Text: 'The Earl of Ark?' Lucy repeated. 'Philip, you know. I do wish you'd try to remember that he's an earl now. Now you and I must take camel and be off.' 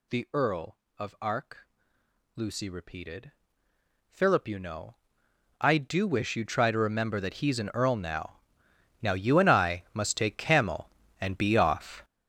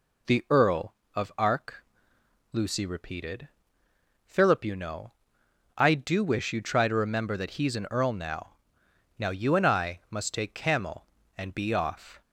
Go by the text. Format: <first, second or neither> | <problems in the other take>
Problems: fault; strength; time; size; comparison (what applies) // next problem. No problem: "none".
second | gets louder; strong; throughout; 11.5 dB